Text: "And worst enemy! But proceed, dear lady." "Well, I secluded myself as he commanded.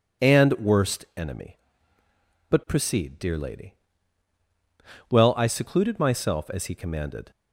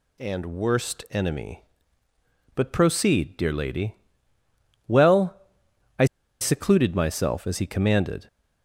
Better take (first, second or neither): first